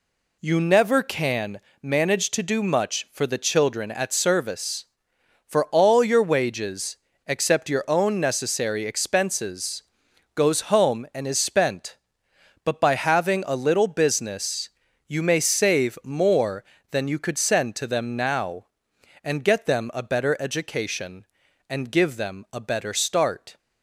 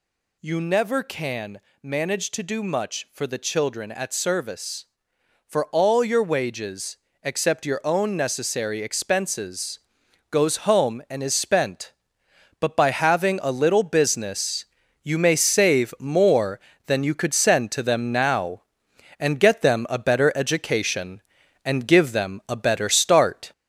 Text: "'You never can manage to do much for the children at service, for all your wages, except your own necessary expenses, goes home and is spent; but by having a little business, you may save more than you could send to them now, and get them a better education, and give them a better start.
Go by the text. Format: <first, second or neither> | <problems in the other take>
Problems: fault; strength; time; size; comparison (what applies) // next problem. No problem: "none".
first | gets louder; noticeable; throughout; 4 dB // pauses between "can" and "manage"; slight; at 1.6 s; 0.22 s long; slight in the first